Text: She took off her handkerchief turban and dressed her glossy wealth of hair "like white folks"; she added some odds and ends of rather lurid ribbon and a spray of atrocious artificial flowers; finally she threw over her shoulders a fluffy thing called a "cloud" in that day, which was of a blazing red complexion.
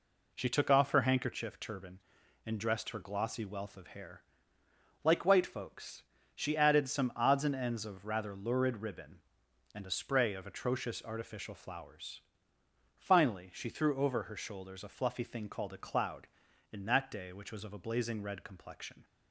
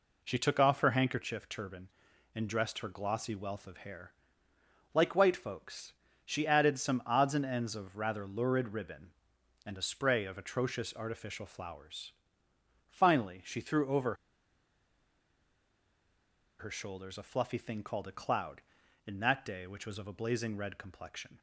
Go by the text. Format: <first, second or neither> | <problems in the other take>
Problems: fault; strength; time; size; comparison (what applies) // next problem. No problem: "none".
first | pauses between "hair" and "like"; noticeable; at 4.1 s; 0.82 s long; noticeable in the first // pauses between "over" and "her"; strong; at 14.1 s; 2.4 s long